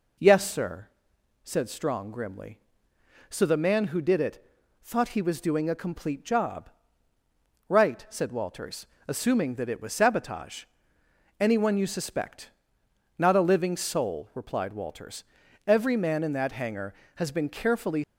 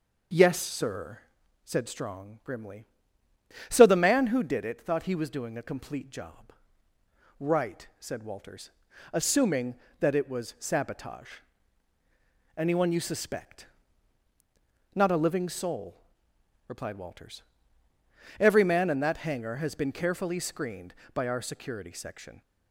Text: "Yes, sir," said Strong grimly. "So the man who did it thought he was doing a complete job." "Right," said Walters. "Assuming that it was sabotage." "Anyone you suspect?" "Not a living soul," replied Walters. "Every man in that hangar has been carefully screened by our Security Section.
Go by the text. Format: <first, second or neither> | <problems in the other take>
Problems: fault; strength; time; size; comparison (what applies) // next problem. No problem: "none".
second | pauses between "it" and "thought"; at 4.4 s; 0.38 s long // stops before "screened by our Security Section"; at 18.0 s